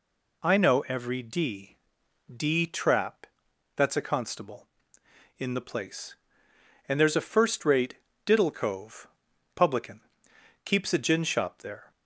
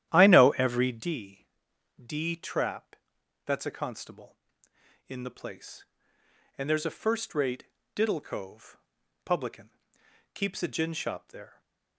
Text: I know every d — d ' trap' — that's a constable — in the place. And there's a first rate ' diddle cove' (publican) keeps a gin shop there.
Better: first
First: none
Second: starts louder than the rest; strong; until 1.2 s; 11.5 dB

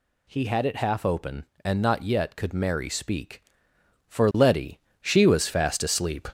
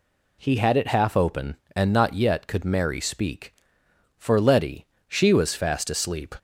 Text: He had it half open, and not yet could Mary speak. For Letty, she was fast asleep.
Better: second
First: gets louder; throughout; 3.5 dB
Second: none

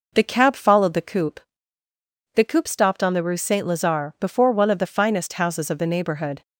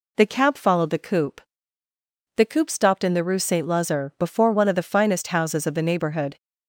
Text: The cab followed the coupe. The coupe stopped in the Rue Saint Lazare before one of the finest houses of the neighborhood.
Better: second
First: says "on" for "in"; at 3.0 s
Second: none

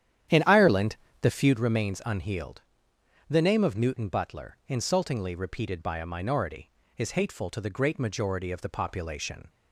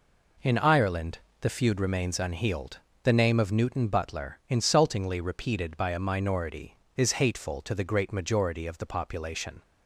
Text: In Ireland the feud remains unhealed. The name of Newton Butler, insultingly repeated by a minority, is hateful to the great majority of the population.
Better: second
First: starts louder than the rest; strong; until 1.6 s; 10.5 dB // pauses between "Ireland" and "the"; slight; at 0.9 s; 0.26 s long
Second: pauses between "Ireland" and "the"; slight; at 1.1 s; 0.22 s long

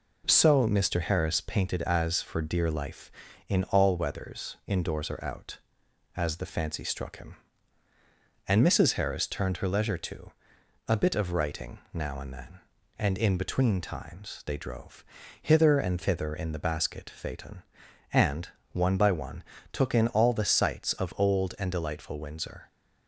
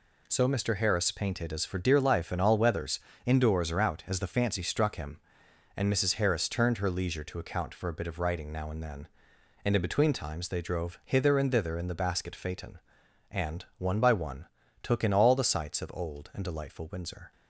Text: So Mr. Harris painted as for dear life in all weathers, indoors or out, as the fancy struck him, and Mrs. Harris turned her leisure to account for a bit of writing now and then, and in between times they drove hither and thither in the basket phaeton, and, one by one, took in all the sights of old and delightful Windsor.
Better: second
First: skips "account for"; at 10.5 s // pauses between "writing" and "now"; slight; at 11.7 s; 0.16 s long // pauses between "drove" and "hither"; slight; at 15.0 s; 0.34 s long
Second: none

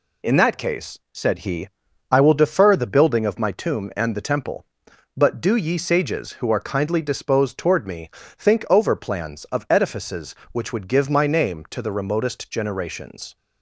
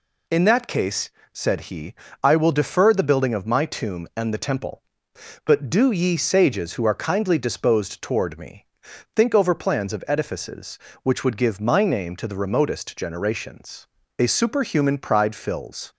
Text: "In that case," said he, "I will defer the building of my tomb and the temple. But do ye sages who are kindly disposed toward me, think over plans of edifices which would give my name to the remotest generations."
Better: first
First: none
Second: goes on to say "A superhuman pride fills"; strong; from 14.1 s on; 1.7 s long

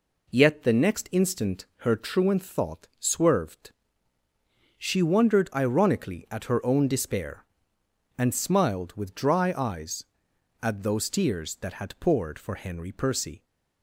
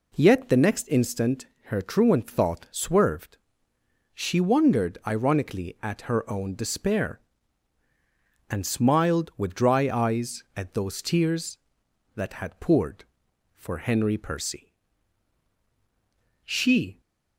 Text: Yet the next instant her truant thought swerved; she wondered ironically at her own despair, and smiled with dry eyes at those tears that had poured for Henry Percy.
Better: first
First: none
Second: pauses between "instant" and "her"; slight; at 1.4 s; 0.20 s long // goes on to say "She"; from 16.4 s on; 0.56 s long

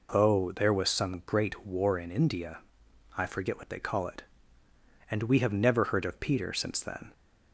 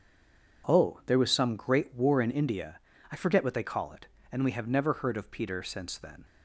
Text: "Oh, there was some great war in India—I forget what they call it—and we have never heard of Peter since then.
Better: first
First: none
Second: stays silent before the first word; slight; until 0.6 s; 0.6 s long

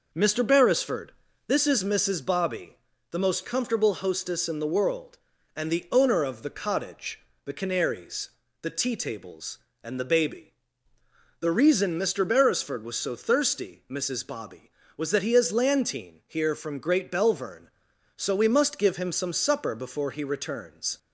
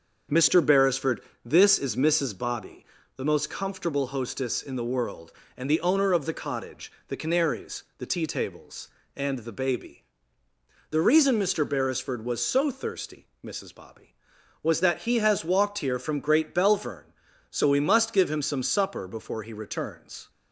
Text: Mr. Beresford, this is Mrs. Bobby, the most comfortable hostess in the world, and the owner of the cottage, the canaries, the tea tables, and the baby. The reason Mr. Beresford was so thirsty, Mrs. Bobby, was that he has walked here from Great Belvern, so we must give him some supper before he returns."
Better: second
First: says "lantine" for "walked"; at 15.4 s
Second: none

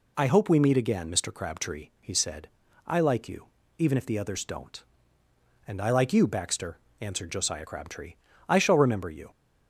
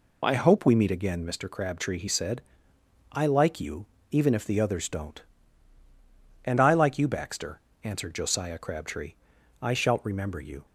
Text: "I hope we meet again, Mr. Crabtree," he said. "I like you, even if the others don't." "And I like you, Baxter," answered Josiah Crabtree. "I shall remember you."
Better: first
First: none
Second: says "shalt" for "shall"; at 9.7 s

